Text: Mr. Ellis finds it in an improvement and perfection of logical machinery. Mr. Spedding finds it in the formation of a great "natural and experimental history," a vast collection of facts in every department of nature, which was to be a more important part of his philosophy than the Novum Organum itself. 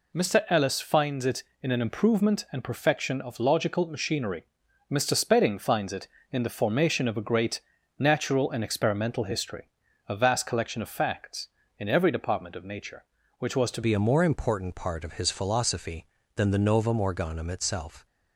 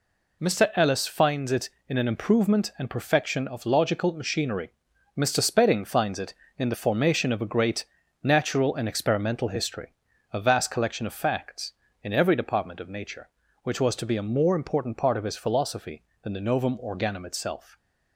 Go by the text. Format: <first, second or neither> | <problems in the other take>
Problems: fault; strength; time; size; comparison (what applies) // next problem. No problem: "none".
second | pauses between "great" and "natural"; at 7.6 s; 0.38 s long; also in the second // changes voice at "be"; from 13.8 s on; 4.2 s long